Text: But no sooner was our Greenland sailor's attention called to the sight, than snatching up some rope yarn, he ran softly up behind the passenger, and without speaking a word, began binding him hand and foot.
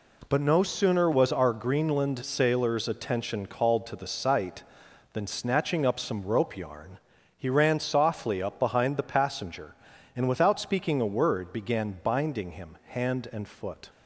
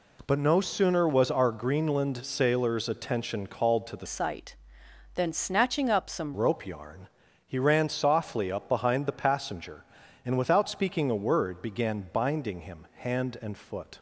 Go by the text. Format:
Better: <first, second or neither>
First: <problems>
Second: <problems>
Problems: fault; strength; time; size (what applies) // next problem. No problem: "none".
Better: first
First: none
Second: changes voice from "sight" to "some"; from 4.0 to 6.3 s; 2.3 s long